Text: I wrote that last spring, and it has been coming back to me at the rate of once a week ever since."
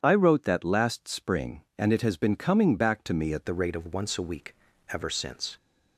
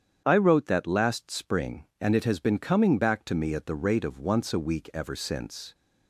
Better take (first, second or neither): second